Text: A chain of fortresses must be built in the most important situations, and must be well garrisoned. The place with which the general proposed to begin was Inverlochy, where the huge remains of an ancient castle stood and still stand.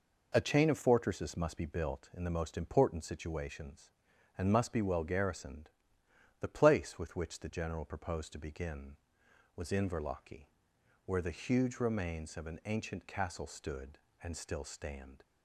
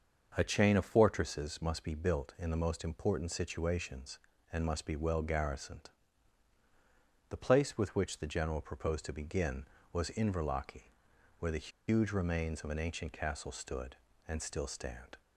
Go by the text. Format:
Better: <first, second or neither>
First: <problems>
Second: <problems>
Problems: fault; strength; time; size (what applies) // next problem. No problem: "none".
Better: first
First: none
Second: starts louder than the rest; until 1.3 s; 6.5 dB // pauses between "the" and "huge"; slight; at 11.6 s; 0.18 s long